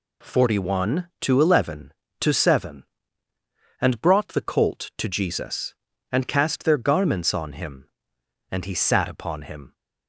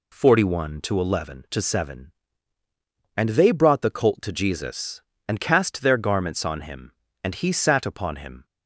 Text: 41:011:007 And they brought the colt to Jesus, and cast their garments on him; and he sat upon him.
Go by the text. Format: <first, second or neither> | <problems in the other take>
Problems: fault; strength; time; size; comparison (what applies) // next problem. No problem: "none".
second | skips "they"; at 3.9 s